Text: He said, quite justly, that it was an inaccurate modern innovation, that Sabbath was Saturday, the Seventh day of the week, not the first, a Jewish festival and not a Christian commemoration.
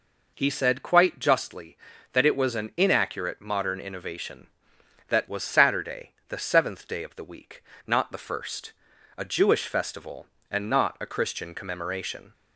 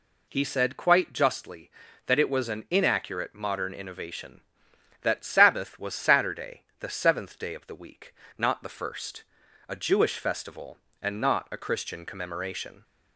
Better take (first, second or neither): second